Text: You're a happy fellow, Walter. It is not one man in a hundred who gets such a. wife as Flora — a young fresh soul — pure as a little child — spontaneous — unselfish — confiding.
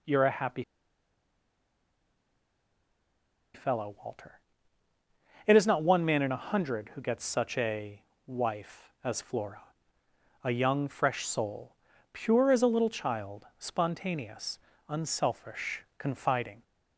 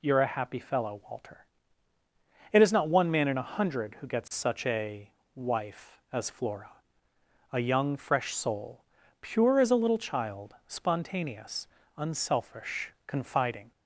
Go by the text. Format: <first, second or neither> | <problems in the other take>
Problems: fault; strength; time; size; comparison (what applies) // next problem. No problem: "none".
second | pauses between "happy" and "fellow"; strong; at 0.6 s; 2.9 s long